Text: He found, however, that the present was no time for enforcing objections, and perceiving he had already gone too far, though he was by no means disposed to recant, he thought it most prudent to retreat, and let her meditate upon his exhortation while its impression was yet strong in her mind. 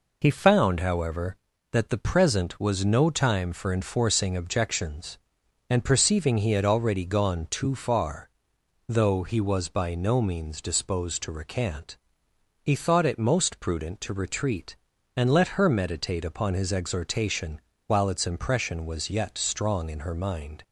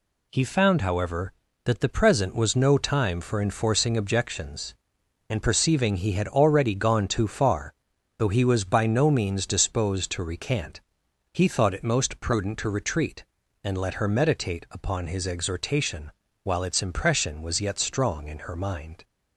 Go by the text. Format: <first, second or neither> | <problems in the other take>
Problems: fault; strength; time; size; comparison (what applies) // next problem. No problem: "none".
neither | pauses between "exhortation" and "while"; slight; the same in both